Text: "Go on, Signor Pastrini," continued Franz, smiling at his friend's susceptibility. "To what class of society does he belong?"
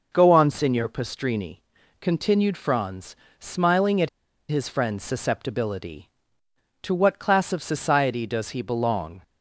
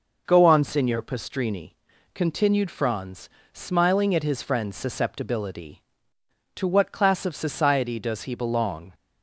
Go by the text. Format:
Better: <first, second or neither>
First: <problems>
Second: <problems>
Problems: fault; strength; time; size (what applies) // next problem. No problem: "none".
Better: second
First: pauses between "at" and "his"; at 4.0 s; 0.41 s long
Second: none